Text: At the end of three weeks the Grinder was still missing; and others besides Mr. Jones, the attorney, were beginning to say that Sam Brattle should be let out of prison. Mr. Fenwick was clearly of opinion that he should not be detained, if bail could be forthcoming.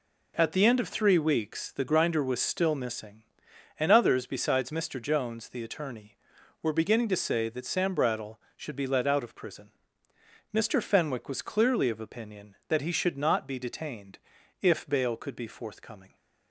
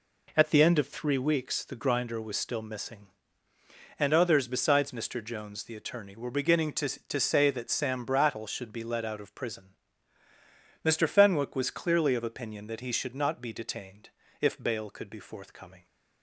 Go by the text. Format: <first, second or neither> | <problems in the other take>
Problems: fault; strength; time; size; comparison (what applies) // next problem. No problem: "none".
first | says "to" twice; at 6.8 s